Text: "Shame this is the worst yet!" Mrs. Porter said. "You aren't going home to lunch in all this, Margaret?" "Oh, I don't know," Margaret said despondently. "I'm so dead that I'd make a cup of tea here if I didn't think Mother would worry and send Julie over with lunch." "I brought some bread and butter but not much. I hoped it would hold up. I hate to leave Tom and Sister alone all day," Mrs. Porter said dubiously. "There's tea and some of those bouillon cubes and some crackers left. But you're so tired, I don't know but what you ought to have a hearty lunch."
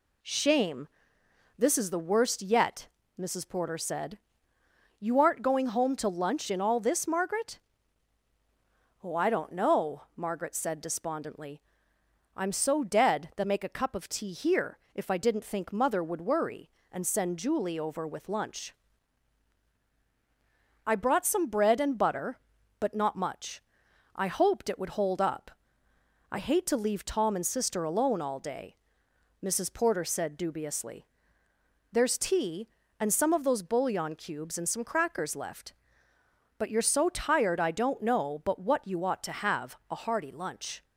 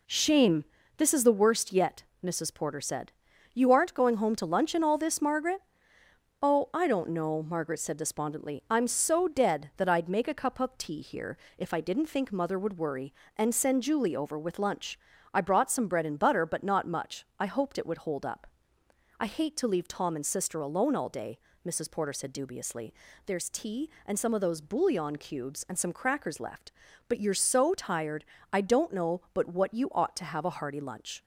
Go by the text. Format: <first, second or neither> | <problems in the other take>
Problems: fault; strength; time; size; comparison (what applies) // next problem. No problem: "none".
second | pauses between "Shame" and "this"; noticeable; at 0.8 s; 0.70 s long; slight in the second // skips "I'd"; at 13.4 s // pauses between "here" and "if"; slight; at 14.7 s; 0.16 s long; slight in the second